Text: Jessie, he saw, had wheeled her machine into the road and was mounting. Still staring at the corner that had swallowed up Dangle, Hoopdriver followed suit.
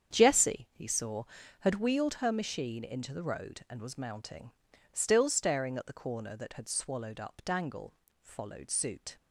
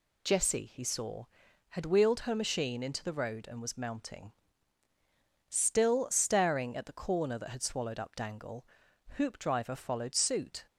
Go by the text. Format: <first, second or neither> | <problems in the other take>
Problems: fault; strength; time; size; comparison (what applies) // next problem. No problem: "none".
second | starts louder than the rest; strong; until 1.1 s; 8 dB // skips "Hoopdriver"; at 8.0 s